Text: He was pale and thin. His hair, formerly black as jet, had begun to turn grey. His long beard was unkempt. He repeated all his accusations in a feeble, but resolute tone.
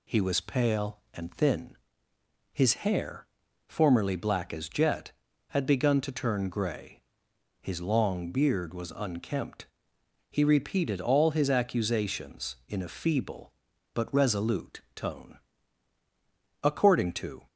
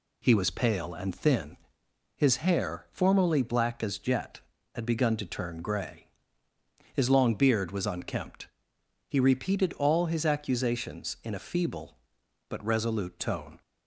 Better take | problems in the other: second | pauses between "resolute" and "tone"; slight; at 14.7 s; 0.16 s long // goes on to say "According to"; noticeable; from 16.6 s on; 0.84 s long

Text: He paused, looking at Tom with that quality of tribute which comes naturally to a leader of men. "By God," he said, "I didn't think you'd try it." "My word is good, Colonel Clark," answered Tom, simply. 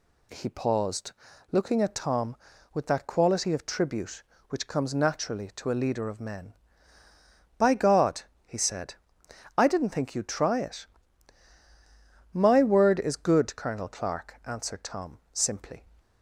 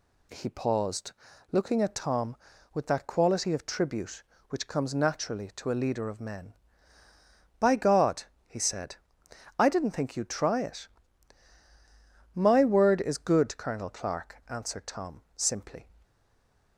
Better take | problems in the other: first | stays silent after the last word; slight; from 16.0 s on; 0.7 s long

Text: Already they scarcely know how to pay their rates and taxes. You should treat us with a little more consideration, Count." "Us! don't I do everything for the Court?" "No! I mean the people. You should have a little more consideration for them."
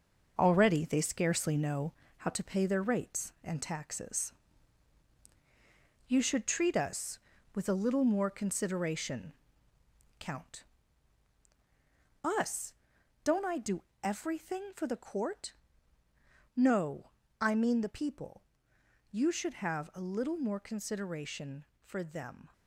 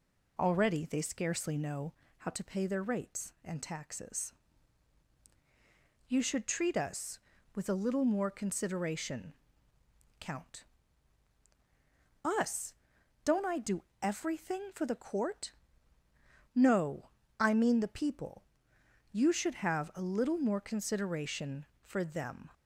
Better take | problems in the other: second | gets quieter; throughout; 7 dB // pauses between "know" and "how"; slight; at 1.9 s; 0.26 s long; slight in the second // pauses between "do" and "everything"; slight; at 13.8 s; 0.20 s long; slight in the second

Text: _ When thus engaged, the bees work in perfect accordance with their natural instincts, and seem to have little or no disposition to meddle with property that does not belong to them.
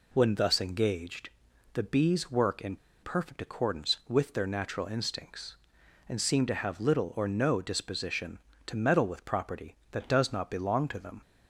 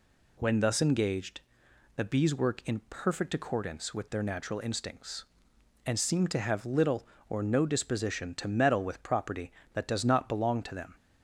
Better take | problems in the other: second | pauses between "in" and "perfect"; slight; at 2.7 s; 0.26 s long

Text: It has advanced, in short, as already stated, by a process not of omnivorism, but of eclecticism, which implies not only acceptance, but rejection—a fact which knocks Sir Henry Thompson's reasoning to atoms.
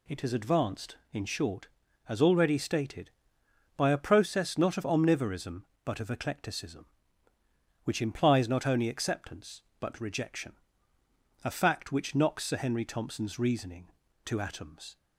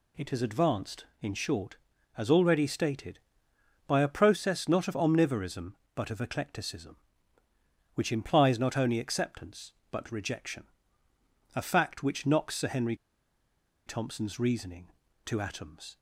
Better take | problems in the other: first | pauses between "Henry" and "Thompson's"; noticeable; at 12.9 s; 0.91 s long

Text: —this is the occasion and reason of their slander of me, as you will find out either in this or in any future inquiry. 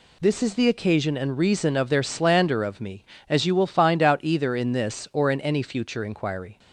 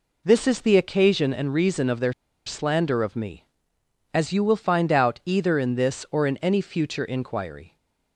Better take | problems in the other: first | pauses between "their" and "slander"; slight; at 2.1 s; 0.35 s long

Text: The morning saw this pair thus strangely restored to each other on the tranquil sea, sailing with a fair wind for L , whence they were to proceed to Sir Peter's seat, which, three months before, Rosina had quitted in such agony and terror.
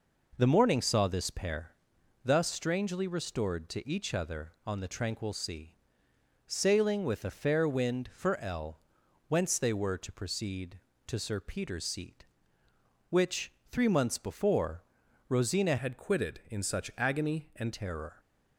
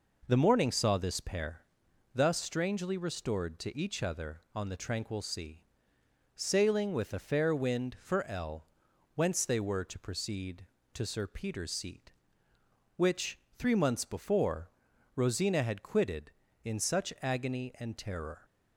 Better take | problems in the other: second | pauses between "pair" and "thus"; noticeable; at 1.6 s; 0.54 s long; noticeable in the second // changes voice from "had" to "and"; from 15.7 to 17.7 s; 2.0 s long

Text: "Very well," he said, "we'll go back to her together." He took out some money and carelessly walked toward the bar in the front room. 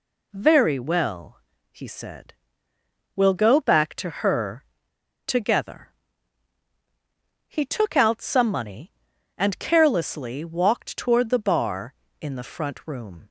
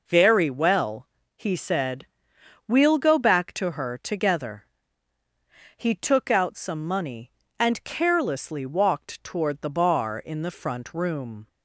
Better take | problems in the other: second | pauses between "her" and "together"; noticeable; at 4.6 s; 0.63 s long

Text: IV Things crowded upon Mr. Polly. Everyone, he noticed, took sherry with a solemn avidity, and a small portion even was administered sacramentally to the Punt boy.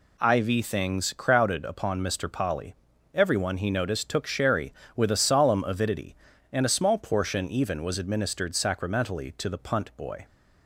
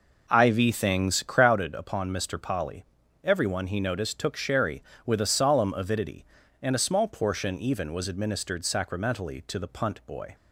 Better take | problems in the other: first | starts louder than the rest; noticeable; until 1.6 s; 5 dB

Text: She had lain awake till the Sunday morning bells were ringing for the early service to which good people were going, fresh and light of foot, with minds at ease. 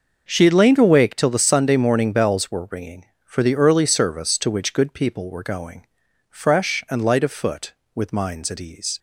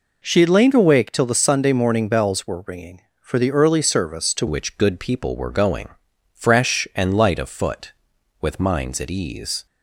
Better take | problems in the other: first | changes voice at "which"; from 4.4 s on; 5.2 s long

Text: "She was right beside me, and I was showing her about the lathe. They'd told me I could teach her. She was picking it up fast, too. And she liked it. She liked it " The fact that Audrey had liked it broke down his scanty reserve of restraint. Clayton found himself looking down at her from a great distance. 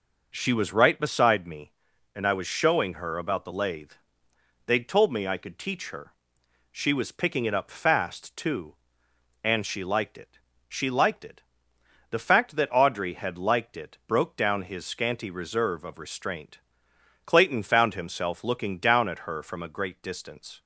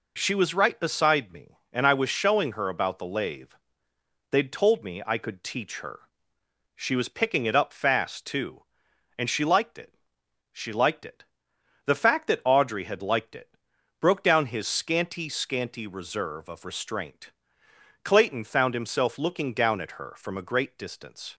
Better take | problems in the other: first | pauses between "it" and "broke"; at 13.5 s; 0.42 s long // says "scanty" twice; at 15.2 s

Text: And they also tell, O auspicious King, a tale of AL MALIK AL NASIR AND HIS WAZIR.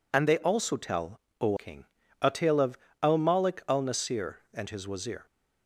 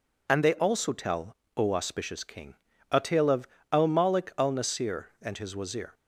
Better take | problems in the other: second | skips "auspicious"; at 1.5 s // pauses between "of" and "AL"; slight; at 2.7 s; 0.24 s long; slight in the second

